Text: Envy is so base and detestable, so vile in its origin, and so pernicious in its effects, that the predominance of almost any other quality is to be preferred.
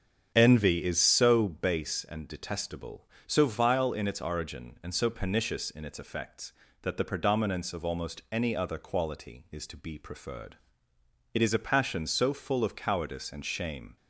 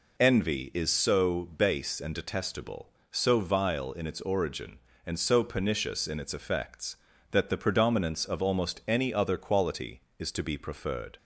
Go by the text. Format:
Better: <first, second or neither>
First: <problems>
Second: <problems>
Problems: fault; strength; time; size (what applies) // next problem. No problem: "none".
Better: second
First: starts louder than the rest; strong; until 1.3 s; 7.5 dB // goes on to say "It is a passion so full of cowardice and shame"; strong; from 11.3 s on; 2.6 s long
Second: none